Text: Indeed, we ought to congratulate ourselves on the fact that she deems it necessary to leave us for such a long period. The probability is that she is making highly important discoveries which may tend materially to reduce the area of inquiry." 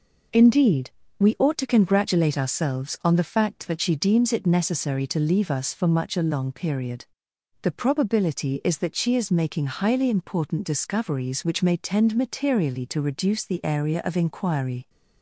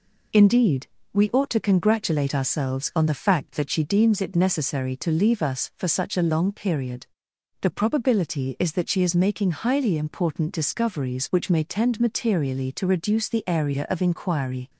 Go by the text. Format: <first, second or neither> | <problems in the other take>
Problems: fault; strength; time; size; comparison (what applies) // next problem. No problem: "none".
second | says "much" for "such"; at 5.8 s